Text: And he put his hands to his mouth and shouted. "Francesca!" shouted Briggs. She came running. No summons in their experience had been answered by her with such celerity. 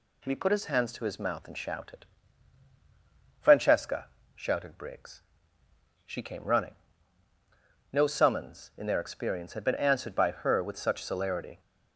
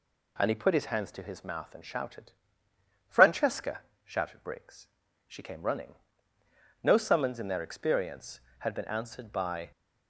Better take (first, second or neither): first